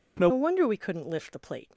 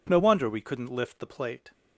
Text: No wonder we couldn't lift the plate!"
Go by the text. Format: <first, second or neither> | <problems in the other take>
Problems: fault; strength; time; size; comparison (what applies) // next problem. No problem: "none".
second | changes voice at "wonder"; from 0.3 s on; 1.4 s long